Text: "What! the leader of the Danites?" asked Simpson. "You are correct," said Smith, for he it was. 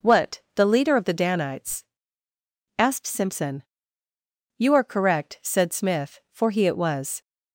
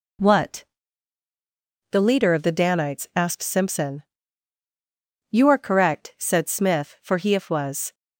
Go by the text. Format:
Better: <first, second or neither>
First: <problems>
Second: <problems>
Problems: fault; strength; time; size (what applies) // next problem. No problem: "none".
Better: first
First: none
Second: says "if" for "it"; at 7.3 s